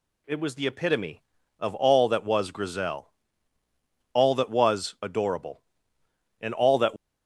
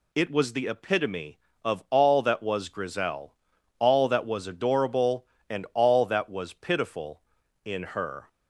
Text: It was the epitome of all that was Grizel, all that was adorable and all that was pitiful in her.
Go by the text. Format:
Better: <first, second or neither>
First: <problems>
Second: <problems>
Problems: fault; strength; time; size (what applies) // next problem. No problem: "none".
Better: second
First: stops before "was pitiful in her"; at 6.9 s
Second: none